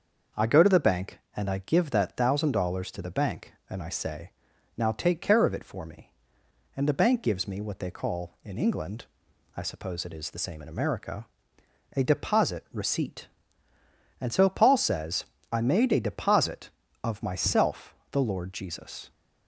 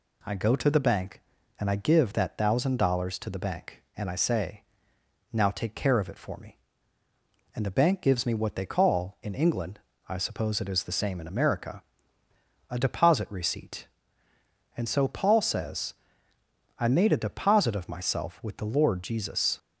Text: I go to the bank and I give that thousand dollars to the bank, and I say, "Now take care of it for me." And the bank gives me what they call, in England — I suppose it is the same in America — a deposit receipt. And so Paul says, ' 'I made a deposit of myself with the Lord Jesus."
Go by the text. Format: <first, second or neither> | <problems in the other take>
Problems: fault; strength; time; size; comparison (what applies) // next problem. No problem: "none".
second | starts louder than the rest; until 1.5 s; 6 dB // skips "with"; at 18.0 s